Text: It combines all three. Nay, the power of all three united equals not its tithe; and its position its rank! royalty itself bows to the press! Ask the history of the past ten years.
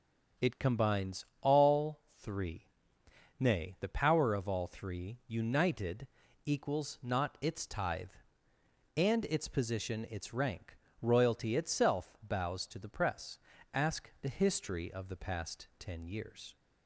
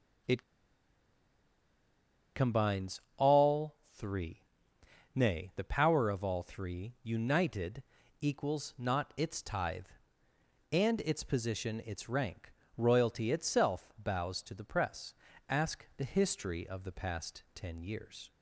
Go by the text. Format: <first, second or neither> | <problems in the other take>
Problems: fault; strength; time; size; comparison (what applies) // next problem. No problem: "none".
first | pauses between "It" and "combines"; strong; at 0.4 s; 1.9 s long // pauses between "combines" and "all"; slight; at 3.0 s; 0.16 s long; slight in the first // pauses between "all" and "three"; slight; at 3.7 s; 0.18 s long; slight in the first // pauses between "united" and "equals"; at 7.8 s; 0.38 s long; also in the first